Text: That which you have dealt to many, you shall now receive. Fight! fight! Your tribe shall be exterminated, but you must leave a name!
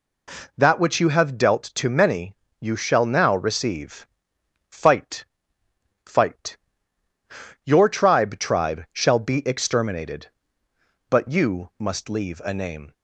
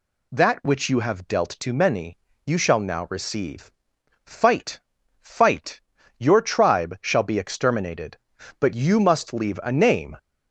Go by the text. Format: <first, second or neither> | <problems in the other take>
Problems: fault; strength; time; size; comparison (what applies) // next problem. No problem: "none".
second | says "tribe" twice; at 8.3 s